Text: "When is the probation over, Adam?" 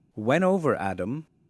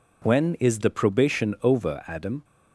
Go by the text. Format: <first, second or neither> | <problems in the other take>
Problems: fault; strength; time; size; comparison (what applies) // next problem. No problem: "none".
second | skips "is the probation"; at 0.4 s